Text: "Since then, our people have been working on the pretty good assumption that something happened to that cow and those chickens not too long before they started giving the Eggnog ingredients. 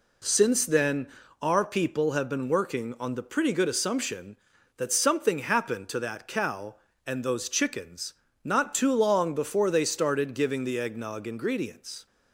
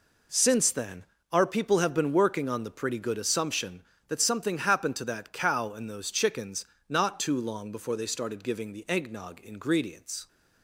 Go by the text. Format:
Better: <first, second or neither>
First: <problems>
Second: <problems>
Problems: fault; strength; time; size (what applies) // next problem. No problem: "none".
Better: neither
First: pauses between "chickens" and "not"; slight; at 8.1 s; 0.30 s long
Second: pauses between "chickens" and "not"; slight; at 6.6 s; 0.22 s long